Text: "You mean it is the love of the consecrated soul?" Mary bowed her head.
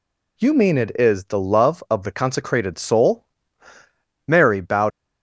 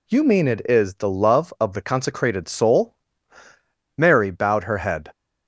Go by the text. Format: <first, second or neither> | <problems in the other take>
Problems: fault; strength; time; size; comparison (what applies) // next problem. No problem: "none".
second | stops before "her head"; at 4.9 s